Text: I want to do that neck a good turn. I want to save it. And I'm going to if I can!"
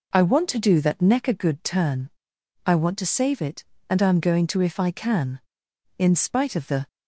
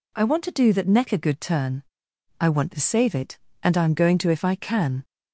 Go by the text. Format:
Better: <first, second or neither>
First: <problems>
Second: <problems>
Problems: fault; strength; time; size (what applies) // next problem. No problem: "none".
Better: second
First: goes on to say "In spite of the"; noticeable; from 5.9 s on; 0.90 s long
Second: none